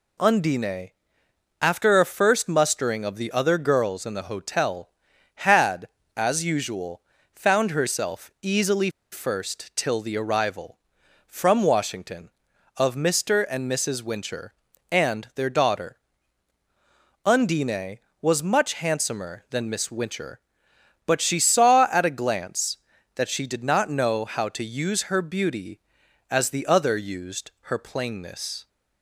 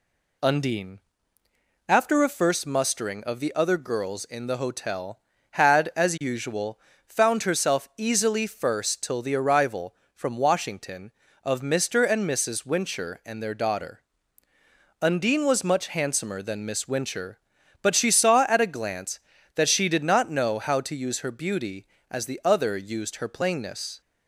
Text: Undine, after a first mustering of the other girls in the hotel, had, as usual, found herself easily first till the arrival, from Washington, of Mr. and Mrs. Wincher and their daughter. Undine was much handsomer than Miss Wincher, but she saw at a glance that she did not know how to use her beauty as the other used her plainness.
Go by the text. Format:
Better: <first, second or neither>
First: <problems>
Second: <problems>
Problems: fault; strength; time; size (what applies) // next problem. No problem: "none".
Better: second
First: pauses between "easily" and "first"; slight; at 8.8 s; 0.22 s long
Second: none